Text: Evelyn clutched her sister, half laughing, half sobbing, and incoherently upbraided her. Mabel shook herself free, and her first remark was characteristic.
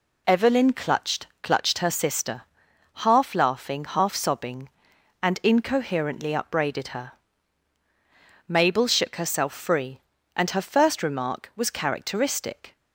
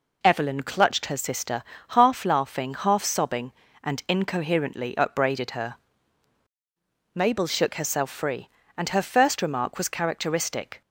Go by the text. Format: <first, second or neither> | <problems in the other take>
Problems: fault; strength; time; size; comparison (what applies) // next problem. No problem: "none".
second | says "clutched" twice; at 1.4 s